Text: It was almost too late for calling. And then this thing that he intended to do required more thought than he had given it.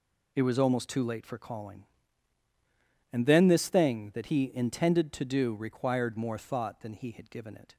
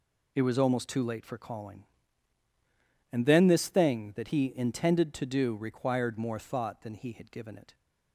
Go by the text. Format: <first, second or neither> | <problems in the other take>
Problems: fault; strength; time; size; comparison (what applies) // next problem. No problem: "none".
neither | none